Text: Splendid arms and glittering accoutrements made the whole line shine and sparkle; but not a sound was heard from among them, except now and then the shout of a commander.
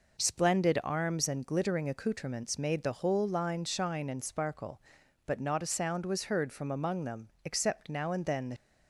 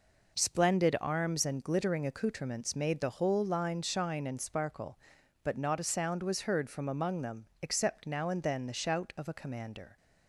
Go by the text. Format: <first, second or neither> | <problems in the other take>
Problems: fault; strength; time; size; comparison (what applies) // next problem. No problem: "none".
second | stops before "shout of a commander"; at 8.5 s